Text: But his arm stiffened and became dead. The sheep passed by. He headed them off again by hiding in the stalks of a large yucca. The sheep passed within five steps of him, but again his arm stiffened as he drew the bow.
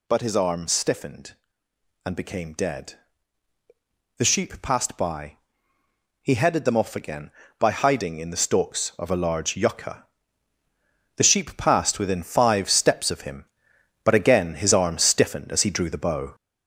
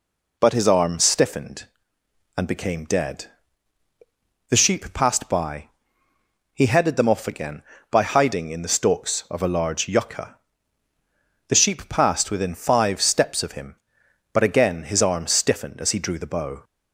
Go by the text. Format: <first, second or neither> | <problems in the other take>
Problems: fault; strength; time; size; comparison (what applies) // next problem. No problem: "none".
second | gets louder; noticeable; throughout; 6 dB